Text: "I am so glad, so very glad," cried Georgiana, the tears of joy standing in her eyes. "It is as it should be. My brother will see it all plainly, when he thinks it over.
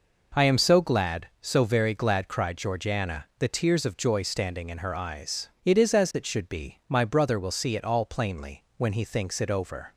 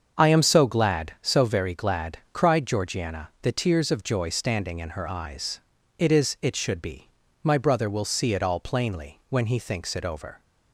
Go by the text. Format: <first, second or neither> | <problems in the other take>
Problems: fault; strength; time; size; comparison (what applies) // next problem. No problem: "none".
first | starts louder than the rest; until 1.2 s; 7 dB // skips "as"; at 6.3 s